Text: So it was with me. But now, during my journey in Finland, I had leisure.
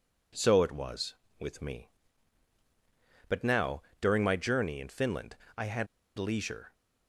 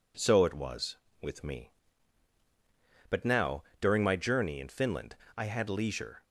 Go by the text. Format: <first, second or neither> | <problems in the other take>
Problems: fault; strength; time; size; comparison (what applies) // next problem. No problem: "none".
second | pauses between "had" and "leisure"; slight; at 5.8 s; 0.32 s long